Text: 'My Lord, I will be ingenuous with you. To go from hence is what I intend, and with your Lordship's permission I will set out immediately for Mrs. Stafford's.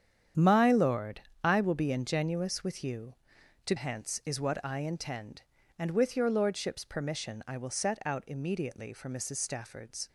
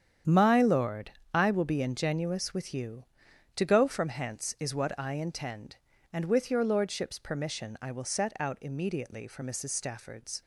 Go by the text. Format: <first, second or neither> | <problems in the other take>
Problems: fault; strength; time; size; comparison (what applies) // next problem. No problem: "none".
second | starts louder than the rest; strong; until 1.5 s; 8.5 dB; strong in the second // skips "go from"; at 3.7 s